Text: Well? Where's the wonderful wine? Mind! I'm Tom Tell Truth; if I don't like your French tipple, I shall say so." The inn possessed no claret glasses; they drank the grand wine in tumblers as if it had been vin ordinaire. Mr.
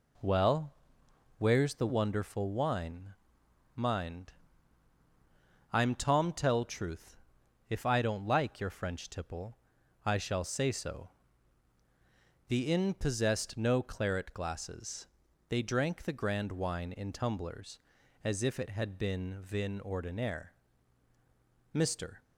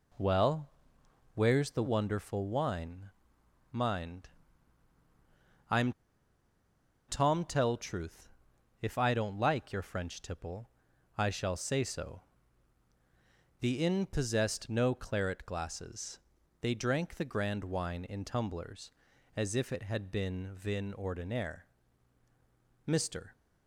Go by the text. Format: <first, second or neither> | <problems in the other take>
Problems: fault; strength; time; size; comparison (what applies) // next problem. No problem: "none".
first | pauses between "I'm" and "Tom"; at 5.9 s; 1.1 s long